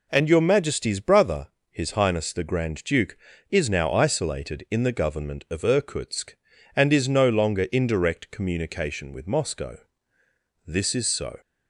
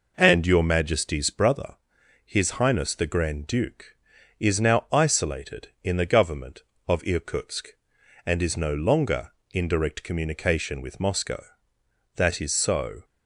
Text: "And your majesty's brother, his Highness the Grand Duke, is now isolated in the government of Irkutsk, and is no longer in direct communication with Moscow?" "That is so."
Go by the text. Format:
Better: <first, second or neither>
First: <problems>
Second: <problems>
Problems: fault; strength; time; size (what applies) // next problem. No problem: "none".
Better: second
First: says "This" for "That"; at 10.6 s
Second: none